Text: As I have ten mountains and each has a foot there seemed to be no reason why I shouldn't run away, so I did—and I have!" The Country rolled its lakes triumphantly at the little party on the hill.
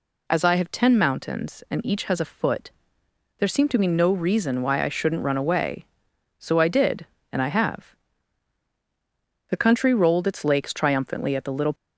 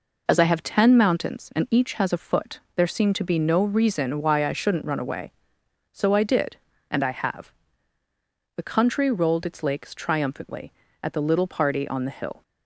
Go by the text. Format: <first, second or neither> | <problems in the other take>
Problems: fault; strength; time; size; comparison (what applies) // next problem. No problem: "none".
second | pauses between "foot" and "there"; noticeable; at 2.7 s; 0.70 s long // stops before "party on the hill"; at 11.7 s